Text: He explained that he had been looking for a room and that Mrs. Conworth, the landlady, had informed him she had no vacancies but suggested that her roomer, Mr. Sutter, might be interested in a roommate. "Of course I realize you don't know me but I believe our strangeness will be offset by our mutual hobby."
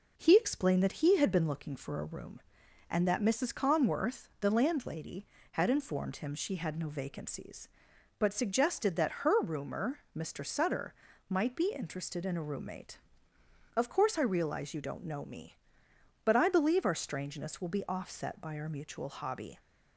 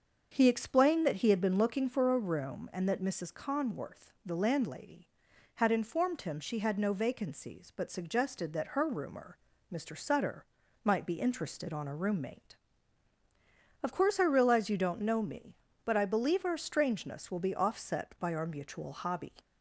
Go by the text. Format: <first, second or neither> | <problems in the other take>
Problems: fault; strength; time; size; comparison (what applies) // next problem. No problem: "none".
first | starts louder than the rest; until 1.3 s; 6.5 dB // says "on" for "in"; at 11.7 s